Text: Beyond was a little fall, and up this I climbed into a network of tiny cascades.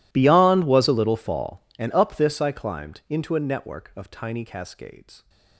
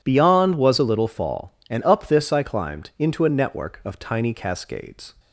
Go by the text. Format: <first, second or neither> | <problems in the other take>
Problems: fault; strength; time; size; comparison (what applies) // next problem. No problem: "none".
second | gets quieter; strong; throughout; 26 dB